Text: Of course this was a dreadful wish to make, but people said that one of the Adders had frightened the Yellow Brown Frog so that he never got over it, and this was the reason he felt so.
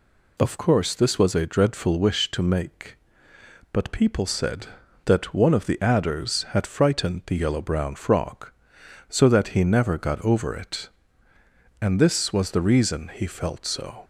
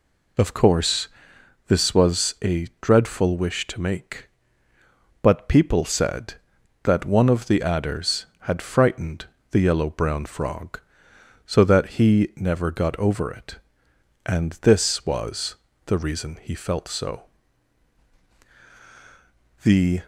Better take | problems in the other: first | pauses between "course" and "this"; noticeable; at 1.0 s; 0.60 s long // pauses between "frightened" and "the"; slight; at 9.2 s; 0.26 s long // pauses between "was" and "the"; slight; at 15.5 s; 0.30 s long // goes on to say "The"; slight; from 19.6 s on; 0.40 s long

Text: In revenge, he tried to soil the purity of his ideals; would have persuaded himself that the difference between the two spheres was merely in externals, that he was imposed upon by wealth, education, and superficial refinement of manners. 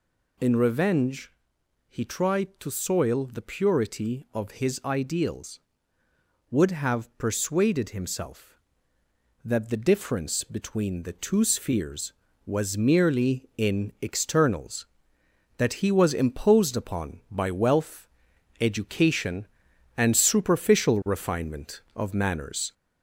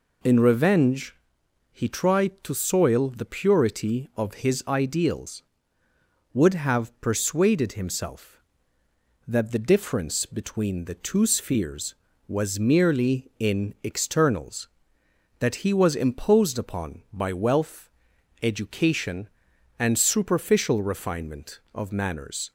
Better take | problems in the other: second | gets louder; slight; throughout; 2.5 dB

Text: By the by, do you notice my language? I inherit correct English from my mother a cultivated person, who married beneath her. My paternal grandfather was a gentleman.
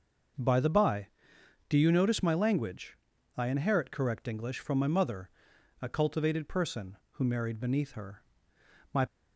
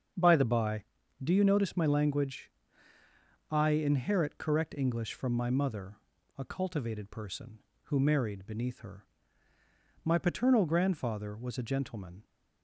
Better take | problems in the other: second | starts louder than the rest; noticeable; until 1.9 s; 6 dB; strong in the second // pauses between "mother" and "a"; noticeable; at 5.2 s; 0.52 s long; also in the second // stops before "paternal grandfather was a gentleman"; at 9.0 s

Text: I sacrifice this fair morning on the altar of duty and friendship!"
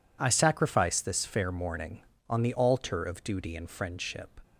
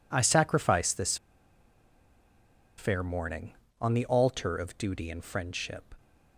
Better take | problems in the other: first | pauses between "this" and "fair"; strong; at 1.1 s; 1.6 s long

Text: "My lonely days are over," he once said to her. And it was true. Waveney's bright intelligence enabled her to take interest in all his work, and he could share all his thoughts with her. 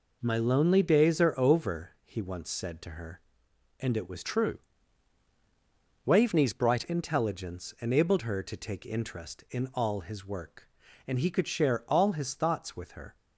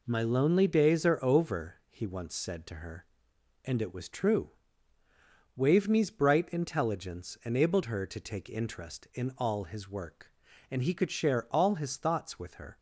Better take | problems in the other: second | changes voice from "true" to "bright"; from 4.2 to 6.8 s; 2.6 s long

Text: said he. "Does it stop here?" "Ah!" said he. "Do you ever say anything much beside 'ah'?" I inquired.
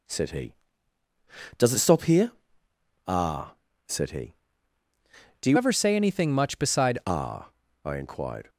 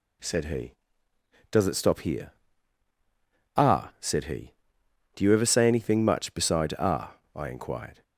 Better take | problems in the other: second | changes voice from "ever" to "beside"; from 5.5 to 6.9 s; 1.4 s long

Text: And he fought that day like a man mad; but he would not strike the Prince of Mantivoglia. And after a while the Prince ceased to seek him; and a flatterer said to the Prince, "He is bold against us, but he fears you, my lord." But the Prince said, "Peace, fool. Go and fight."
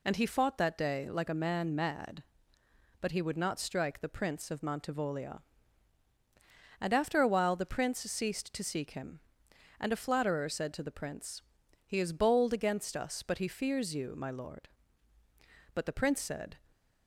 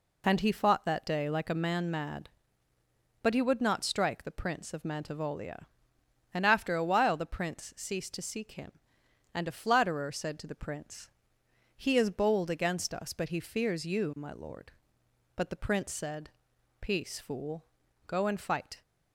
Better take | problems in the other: second | stops before "Peace fool Go and fight"; at 16.7 s

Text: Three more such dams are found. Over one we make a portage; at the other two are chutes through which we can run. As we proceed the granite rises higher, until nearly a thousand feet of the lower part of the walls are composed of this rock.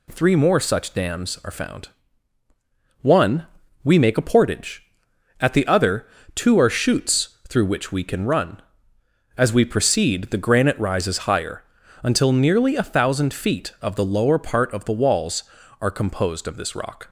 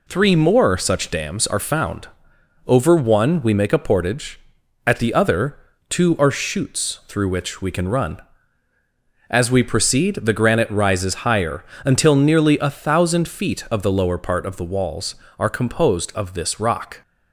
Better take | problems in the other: second | skips "Over"; at 2.4 s // pauses between "one" and "we"; at 3.4 s; 0.40 s long // pauses between "other" and "two"; slight; at 6.0 s; 0.26 s long; slight in the second

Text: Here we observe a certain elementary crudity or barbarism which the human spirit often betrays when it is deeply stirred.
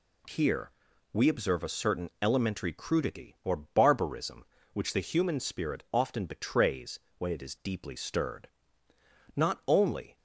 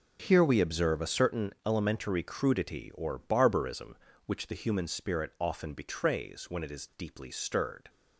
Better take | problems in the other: second | pauses between "Here" and "we"; at 0.6 s; 0.44 s long // pauses between "betrays" and "when"; slight; at 6.9 s; 0.18 s long // goes on to say "Not only"; noticeable; from 9.3 s on; 0.82 s long

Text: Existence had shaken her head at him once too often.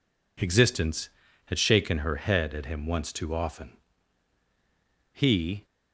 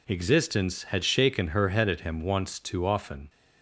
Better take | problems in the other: second | goes on to say "He"; from 5.1 s on; 0.54 s long

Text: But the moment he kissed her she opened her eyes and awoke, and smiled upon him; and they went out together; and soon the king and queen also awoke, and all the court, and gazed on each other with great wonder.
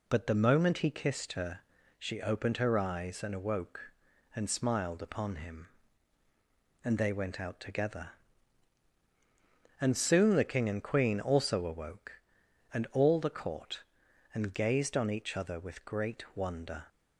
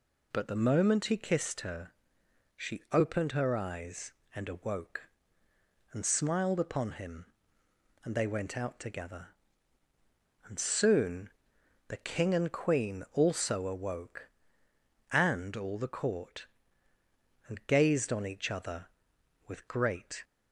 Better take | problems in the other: first | pauses between "her" and "she"; noticeable; at 1.9 s; 0.64 s long; also in the first // pauses between "soon" and "the"; noticeable; at 11.2 s; 0.58 s long // stops before "wonder"; at 20.2 s

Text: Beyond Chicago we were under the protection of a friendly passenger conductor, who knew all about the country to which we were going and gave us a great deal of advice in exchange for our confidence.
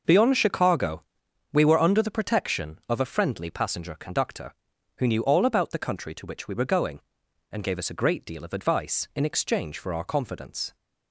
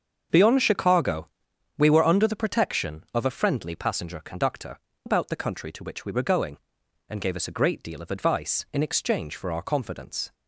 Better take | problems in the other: first | starts louder than the rest; until 1.8 s; 6.5 dB // pauses between "Chicago" and "we"; noticeable; at 1.2 s; 0.50 s long; noticeable in the first // skips "who knew all"; at 4.9 s

